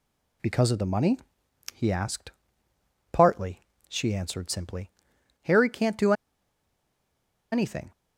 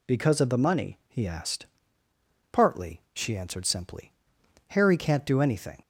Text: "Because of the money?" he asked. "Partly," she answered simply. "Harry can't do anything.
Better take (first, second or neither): second